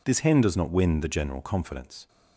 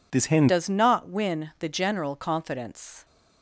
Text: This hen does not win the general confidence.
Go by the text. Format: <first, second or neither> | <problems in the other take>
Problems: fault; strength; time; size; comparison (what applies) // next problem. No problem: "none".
first | changes voice at "does"; from 0.4 s on; 2.6 s long